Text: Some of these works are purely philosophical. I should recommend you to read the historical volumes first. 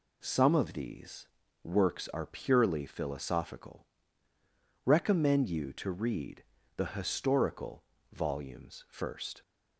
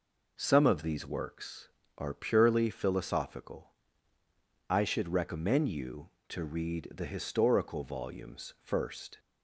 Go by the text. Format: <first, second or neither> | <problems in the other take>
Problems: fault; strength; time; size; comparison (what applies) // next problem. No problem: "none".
second | pauses between "these" and "works"; at 1.2 s; 0.38 s long // skips "I should"; at 4.3 s // pauses between "read" and "the"; slight; at 6.4 s; 0.32 s long // pauses between "historical" and "volumes"; slight; at 7.8 s; 0.30 s long